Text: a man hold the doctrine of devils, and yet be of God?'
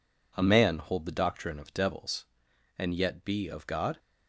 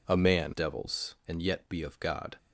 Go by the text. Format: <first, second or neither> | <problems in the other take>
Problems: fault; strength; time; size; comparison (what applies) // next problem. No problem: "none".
first | skips "hold the doctrine of"; at 0.5 s